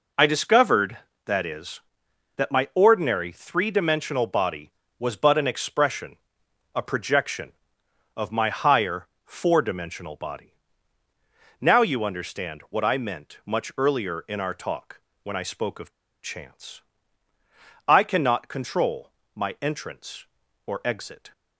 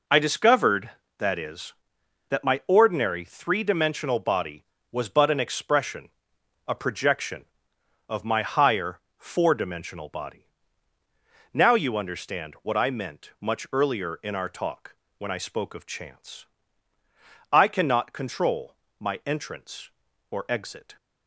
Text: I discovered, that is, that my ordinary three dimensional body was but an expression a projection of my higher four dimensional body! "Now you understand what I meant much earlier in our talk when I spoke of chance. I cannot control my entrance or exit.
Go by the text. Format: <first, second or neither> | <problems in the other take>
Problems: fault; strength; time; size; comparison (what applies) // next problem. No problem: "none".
second | pauses between "expression" and "a"; noticeable; at 6.1 s; 0.58 s long; noticeable in the second // pauses between "higher" and "four"; slight; at 9.0 s; 0.20 s long; slight in the second // pauses between "talk" and "when"; slight; at 14.9 s; 0.24 s long; slight in the second // pauses between "of" and "chance"; slight; at 15.9 s; 0.31 s long // pauses between "control" and "my"; slight; at 19.1 s; 0.22 s long; slight in the second